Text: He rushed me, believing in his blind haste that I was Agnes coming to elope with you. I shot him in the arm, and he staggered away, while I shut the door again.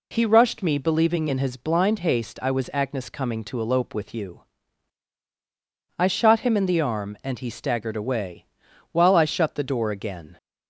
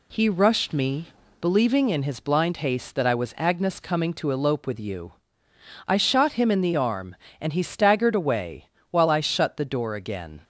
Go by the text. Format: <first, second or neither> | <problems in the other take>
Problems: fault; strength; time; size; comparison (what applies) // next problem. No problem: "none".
second | skips "that"; at 2.3 s